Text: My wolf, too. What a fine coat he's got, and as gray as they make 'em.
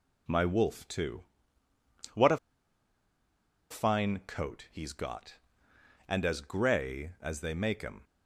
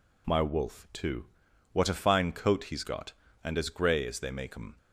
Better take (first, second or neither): second